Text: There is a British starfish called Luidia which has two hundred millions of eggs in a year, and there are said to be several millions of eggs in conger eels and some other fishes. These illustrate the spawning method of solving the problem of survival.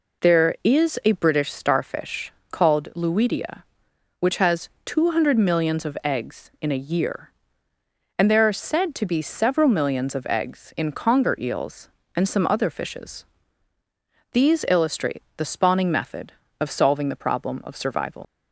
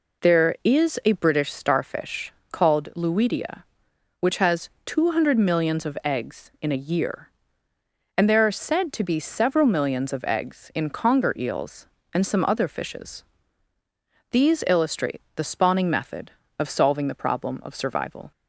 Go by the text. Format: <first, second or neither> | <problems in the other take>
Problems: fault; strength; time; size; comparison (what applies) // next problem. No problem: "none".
second | pauses between "starfish" and "called"; slight; at 2.3 s; 0.18 s long; slight in the second // pauses between "has" and "two"; slight; at 4.6 s; 0.16 s long; slight in the second // leaves "survival" unfinished; at 18.2 s; 70 ms